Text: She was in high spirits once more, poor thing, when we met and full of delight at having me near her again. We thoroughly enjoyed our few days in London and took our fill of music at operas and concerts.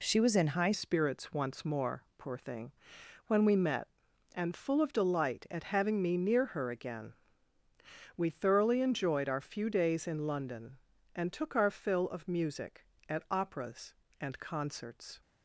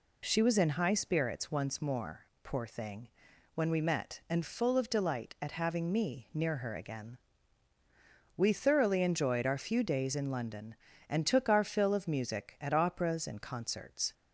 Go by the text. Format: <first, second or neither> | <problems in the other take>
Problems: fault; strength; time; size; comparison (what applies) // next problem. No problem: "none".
second | changes voice at "spirits"; from 0.7 s on; 14.5 s long